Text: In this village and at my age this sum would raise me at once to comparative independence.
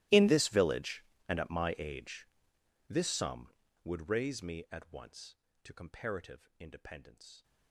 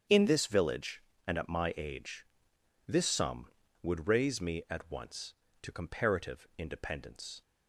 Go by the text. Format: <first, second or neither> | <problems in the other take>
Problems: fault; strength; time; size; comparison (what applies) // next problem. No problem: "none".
second | gets quieter; strong; throughout; 24 dB // starts louder than the rest; strong; until 1.3 s; 16.5 dB; strong in the second // pauses between "age" and "this"; noticeable; at 2.2 s; 0.62 s long; noticeable in the second